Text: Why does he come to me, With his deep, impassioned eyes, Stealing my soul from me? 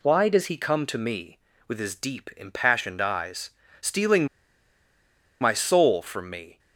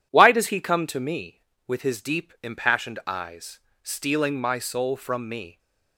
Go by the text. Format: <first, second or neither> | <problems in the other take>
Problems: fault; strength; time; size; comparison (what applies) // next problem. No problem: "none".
second | pauses between "Stealing" and "my"; at 4.2 s; 1.1 s long